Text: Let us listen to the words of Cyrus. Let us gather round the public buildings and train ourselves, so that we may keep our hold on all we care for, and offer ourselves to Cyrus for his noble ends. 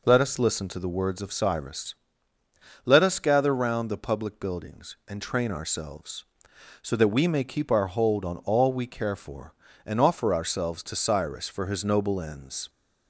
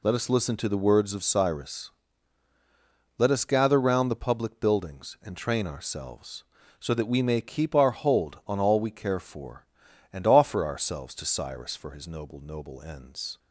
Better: first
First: none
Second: says "noble" twice; at 12.4 s

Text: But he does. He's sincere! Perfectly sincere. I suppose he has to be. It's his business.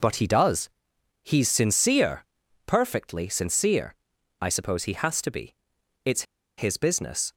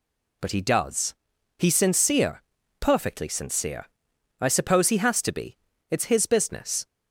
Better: second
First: pauses between "It's" and "his"; slight; at 6.2 s; 0.34 s long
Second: none

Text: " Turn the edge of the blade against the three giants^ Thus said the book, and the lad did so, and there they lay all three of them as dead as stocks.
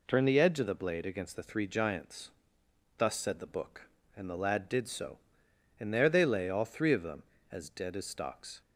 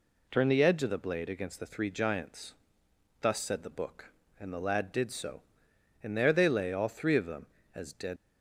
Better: first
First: pauses between "giants" and "Thus"; noticeable; at 2.2 s; 0.70 s long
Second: pauses between "giants" and "Thus"; noticeable; at 2.5 s; 0.70 s long // stops before "as stocks"; at 8.1 s

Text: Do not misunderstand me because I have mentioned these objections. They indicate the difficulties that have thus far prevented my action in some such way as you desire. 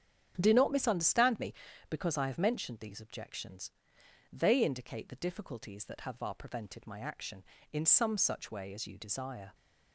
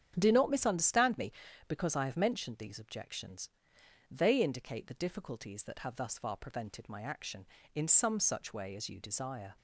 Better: second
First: starts louder than the rest; strong; until 1.3 s; 9 dB // skips "thus"; at 6.1 s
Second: starts louder than the rest; strong; until 1.1 s; 9 dB

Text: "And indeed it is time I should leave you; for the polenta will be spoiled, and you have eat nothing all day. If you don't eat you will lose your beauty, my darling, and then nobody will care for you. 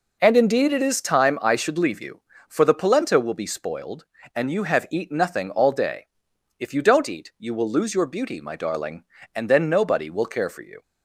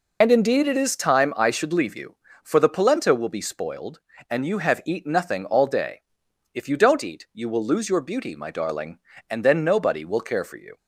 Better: first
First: none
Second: loses the start of "And"; at 0.2 s; 55 ms

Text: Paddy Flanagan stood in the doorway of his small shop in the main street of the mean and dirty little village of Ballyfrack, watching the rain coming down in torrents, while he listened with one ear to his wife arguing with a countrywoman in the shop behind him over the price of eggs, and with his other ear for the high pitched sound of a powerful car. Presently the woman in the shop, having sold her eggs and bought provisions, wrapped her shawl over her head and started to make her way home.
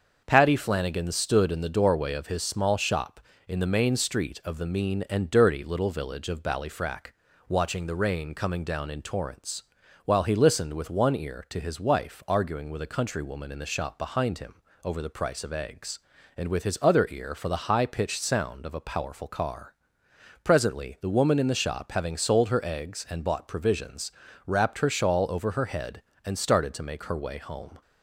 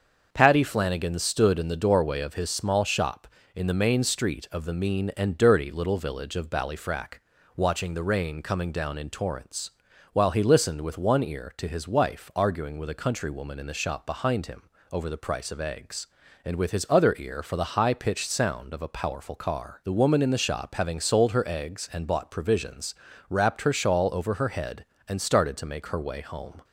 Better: first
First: starts louder than the rest; until 1.2 s; 6.5 dB // pauses between "him" and "over"; slight; at 14.5 s; 0.30 s long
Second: starts louder than the rest; until 1.3 s; 6.5 dB // pauses between "him" and "over"; slight; at 14.6 s; 0.30 s long // skips "Presently"; at 19.8 s

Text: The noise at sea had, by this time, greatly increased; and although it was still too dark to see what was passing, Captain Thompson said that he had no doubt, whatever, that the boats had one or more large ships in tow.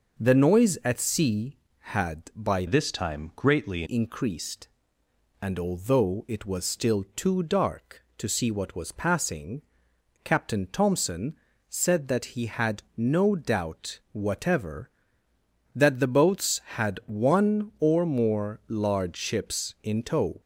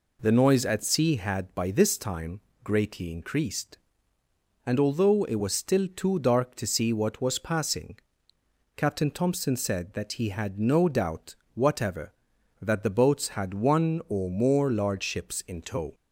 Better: second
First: starts louder than the rest; noticeable; until 1.2 s; 6 dB // changes voice from "this" to "greatly"; from 2.6 to 3.8 s; 1.2 s long // pauses between "Thompson" and "said"; slight; at 11.3 s; 0.32 s long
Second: none

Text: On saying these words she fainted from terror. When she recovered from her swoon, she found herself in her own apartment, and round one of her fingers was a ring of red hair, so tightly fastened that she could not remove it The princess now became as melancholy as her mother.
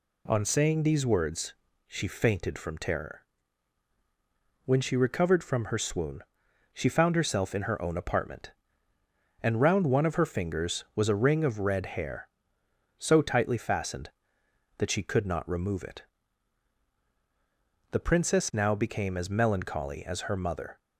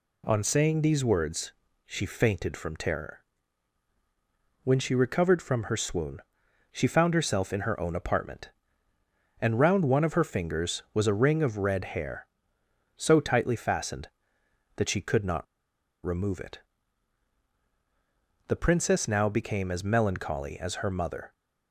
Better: first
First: pauses between "words" and "she"; slight; at 1.5 s; 0.32 s long // pauses between "it" and "The"; strong; at 16.0 s; 1.9 s long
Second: pauses between "words" and "she"; slight; at 1.5 s; 0.32 s long // pauses between "not" and "remove"; noticeable; at 15.4 s; 0.59 s long // pauses between "it" and "The"; strong; at 16.5 s; 1.9 s long

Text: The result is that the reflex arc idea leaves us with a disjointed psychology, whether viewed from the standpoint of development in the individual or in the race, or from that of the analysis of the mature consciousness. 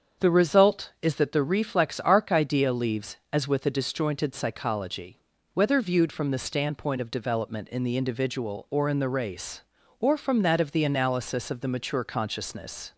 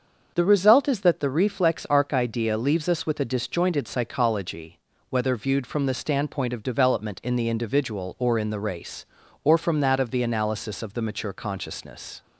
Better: second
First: starts louder than the rest; strong; until 1.3 s; 7 dB // says "as" for "us"; at 3.3 s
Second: starts louder than the rest; until 1.3 s; 6.5 dB

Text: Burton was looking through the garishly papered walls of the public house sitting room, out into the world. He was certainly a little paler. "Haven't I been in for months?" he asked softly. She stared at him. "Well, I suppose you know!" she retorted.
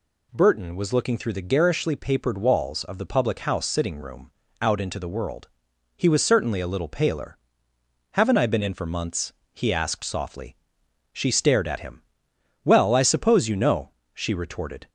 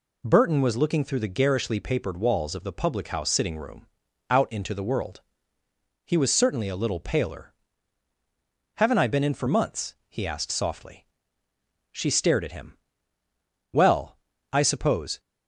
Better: first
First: none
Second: stops before "you know she retorted"; at 15.1 s

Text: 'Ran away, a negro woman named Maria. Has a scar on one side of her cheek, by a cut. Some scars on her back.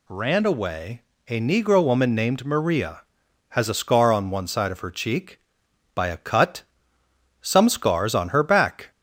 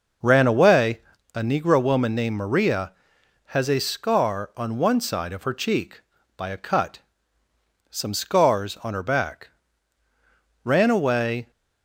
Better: first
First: none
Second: goes on to say "Ran away"; noticeable; from 10.6 s on; 0.88 s long

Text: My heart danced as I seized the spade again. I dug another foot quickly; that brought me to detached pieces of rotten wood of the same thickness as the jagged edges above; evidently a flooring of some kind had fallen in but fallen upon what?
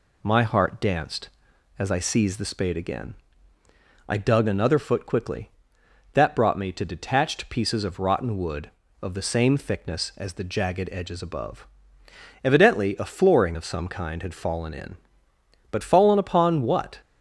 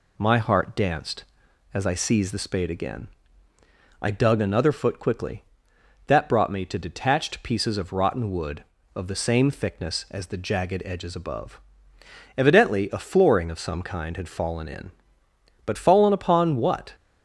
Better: neither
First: none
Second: none

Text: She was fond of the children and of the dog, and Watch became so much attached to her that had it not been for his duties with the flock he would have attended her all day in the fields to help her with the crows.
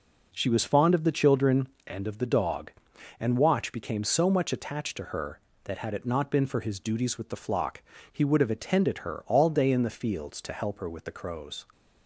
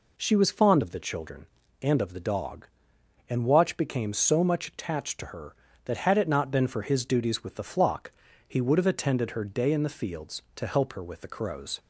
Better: first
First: pauses between "flock" and "he"; slight; at 7.8 s; 0.28 s long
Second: pauses between "flock" and "he"; slight; at 8.1 s; 0.34 s long // skips "all"; at 9.4 s

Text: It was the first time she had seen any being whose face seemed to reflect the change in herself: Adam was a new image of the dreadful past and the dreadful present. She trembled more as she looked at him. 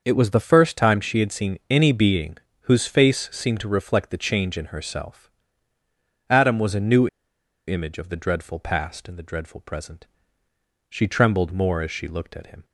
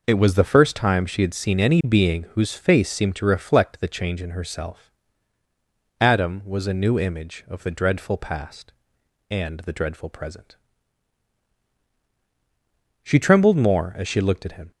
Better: second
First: starts louder than the rest; until 1.0 s; 6 dB // pauses between "being" and "whose"; slight; at 2.3 s; 0.26 s long // pauses between "new" and "image"; noticeable; at 7.0 s; 0.61 s long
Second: none

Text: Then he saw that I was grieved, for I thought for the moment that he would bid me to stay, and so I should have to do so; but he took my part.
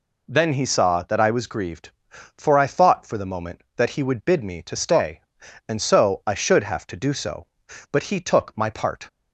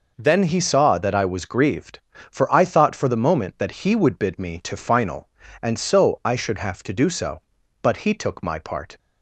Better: first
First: none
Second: says "final" for "stay"; at 4.7 s

